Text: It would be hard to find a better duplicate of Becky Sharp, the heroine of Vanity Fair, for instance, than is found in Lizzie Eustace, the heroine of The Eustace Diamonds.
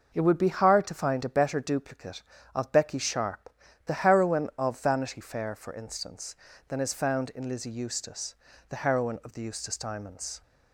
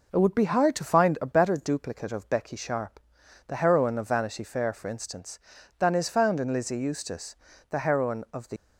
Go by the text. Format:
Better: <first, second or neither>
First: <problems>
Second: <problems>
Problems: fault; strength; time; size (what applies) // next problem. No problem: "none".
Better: first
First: none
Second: stops before "Eustace Diamonds"; at 8.5 s